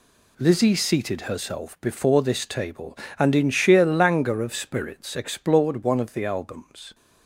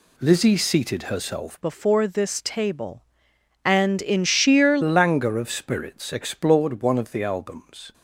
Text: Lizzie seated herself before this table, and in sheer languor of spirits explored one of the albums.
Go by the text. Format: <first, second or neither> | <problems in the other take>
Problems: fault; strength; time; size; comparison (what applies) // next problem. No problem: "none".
first | changes voice from "before" to "sheer"; from 1.6 to 4.7 s; 3.1 s long